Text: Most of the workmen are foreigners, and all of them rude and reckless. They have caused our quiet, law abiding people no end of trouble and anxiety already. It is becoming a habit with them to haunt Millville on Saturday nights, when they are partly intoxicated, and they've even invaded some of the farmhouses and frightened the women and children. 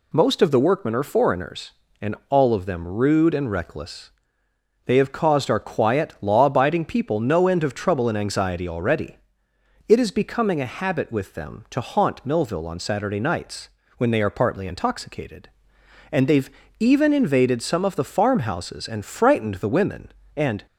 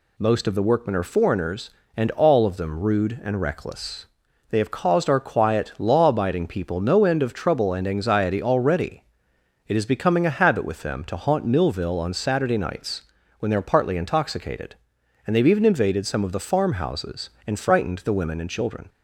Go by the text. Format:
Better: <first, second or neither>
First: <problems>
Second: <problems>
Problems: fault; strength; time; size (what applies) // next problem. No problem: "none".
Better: second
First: pauses between "they've" and "even"; slight; at 16.4 s; 0.28 s long // stops before "children"; at 20.6 s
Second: none